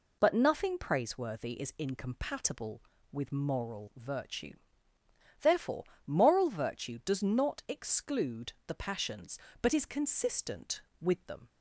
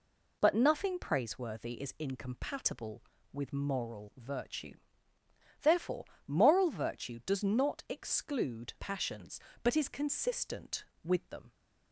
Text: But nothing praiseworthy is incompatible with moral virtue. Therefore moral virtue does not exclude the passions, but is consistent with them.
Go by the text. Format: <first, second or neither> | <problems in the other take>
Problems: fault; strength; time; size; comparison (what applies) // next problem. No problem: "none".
first | pauses between "Therefore" and "moral"; slight; at 6.0 s; 0.22 s long; slight in the first // skips "the"; at 8.7 s